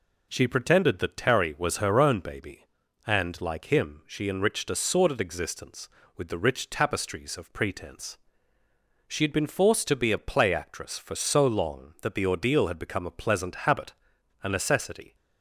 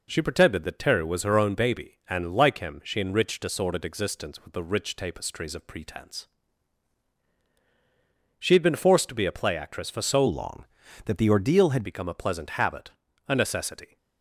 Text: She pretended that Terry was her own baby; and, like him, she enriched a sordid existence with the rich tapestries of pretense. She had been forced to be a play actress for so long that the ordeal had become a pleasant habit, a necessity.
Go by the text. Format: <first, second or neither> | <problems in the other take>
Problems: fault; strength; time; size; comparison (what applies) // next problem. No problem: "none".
first | changes voice from "long" to "had"; from 10.2 to 11.8 s; 1.6 s long